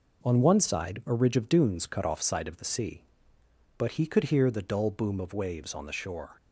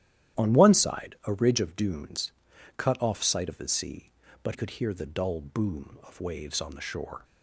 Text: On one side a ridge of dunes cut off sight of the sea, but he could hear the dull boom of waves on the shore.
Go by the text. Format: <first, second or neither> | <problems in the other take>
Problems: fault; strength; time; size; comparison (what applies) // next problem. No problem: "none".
first | starts louder than the rest; strong; until 1.4 s; 12 dB // pauses between "dunes" and "cut"; at 2.3 s; 0.44 s long // skips "he"; at 4.5 s